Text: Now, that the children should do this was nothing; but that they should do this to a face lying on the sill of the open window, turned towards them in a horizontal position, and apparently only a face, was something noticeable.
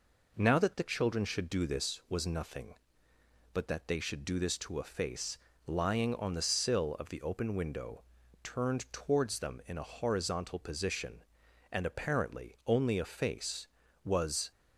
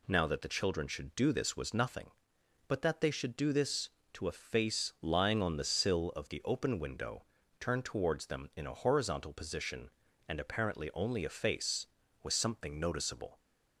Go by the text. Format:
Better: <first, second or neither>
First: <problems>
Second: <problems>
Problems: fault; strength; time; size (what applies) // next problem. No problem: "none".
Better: second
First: pauses between "face" and "lying"; slight; at 5.3 s; 0.26 s long // stops before "something noticeable"; at 14.5 s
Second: none